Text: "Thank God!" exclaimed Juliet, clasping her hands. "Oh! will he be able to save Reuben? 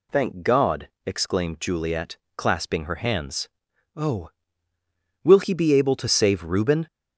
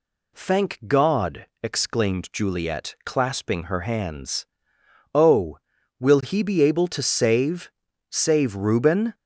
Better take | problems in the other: first | says "save" twice; at 8.1 s

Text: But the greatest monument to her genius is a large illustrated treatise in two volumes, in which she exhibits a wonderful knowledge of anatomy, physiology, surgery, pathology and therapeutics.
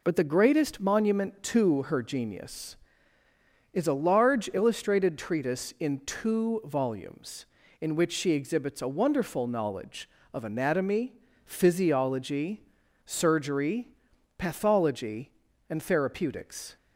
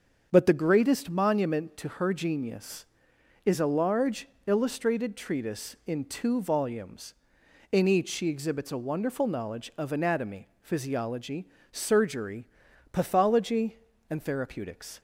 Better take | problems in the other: first | starts louder than the rest; until 1.3 s; 7 dB // pauses between "large" and "illustrated"; slight; at 4.2 s; 0.18 s long // says "each" for "which"; at 7.8 s

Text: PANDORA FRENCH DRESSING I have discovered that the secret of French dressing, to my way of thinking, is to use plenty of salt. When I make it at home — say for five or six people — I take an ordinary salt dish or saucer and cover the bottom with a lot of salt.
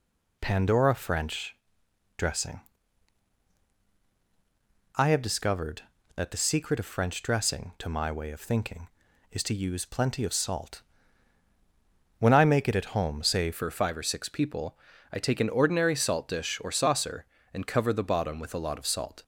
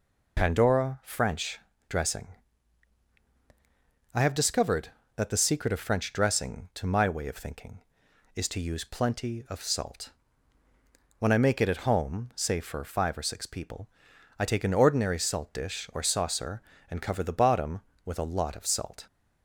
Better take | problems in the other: second | pauses between "FRENCH" and "DRESSING"; noticeable; at 1.5 s; 0.62 s long; slight in the second // pauses between "DRESSING" and "I"; strong; at 2.6 s; 2.3 s long; strong in the second // changes voice at "for"; from 13.5 s on; 5.7 s long

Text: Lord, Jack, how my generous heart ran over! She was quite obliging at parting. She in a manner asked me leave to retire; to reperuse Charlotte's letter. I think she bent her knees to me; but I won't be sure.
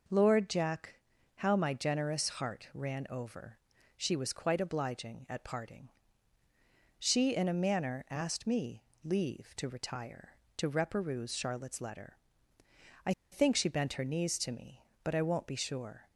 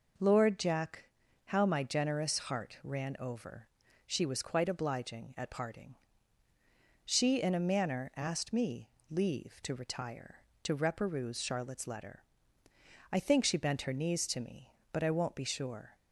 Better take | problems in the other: second | pauses between "me" and "leave"; slight; at 8.8 s; 0.20 s long; slight in the second // pauses between "I" and "think"; slight; at 13.1 s; 0.20 s long

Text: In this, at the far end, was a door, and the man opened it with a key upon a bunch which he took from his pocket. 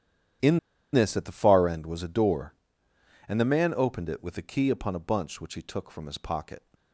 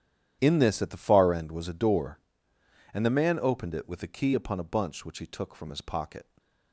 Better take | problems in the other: second | starts louder than the rest; strong; until 1.7 s; 10 dB; strong in the second // pauses between "In" and "this"; slight; at 0.5 s; 0.34 s long

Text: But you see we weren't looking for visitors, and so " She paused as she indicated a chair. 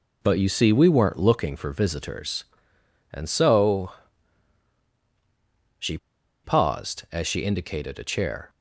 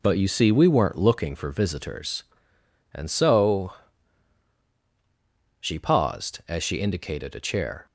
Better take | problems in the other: second | pauses between "She" and "paused"; noticeable; at 5.9 s; 0.47 s long

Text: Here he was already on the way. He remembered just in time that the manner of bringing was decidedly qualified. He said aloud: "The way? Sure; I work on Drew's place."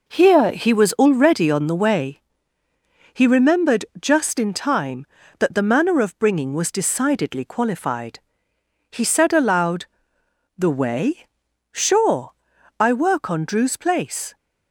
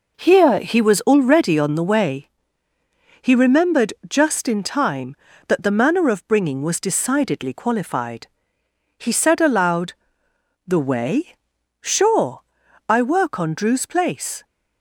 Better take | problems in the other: neither | pauses between "remembered" and "just"; slight; the same in both

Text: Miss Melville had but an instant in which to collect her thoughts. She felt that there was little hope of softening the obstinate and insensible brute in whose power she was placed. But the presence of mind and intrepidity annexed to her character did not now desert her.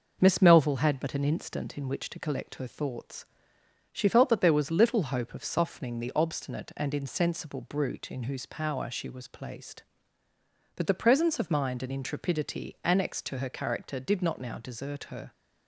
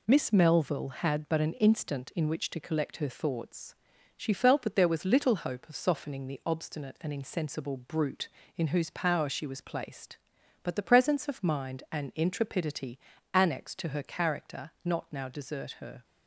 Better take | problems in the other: first | pauses between "intrepidity" and "annexed"; slight; at 12.9 s; 0.34 s long // skips "did"; at 14.7 s

